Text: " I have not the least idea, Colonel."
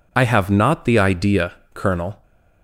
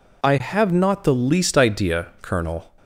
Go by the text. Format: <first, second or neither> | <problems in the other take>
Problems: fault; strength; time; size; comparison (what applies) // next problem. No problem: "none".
second | skips "least"; at 0.9 s